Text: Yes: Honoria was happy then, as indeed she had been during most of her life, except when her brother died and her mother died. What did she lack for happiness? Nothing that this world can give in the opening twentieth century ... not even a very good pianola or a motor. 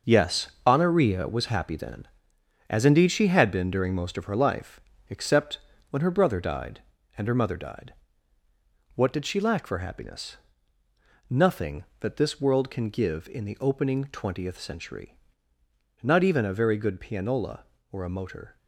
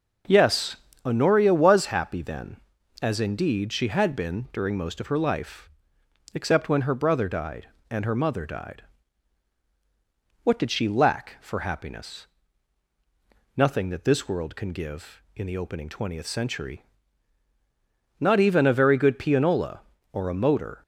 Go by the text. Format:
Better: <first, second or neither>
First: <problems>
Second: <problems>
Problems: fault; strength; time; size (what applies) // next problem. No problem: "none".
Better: second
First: gets quieter; strong; throughout; 8.5 dB // pauses between "except" and "when"; slight; at 5.5 s; 0.30 s long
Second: none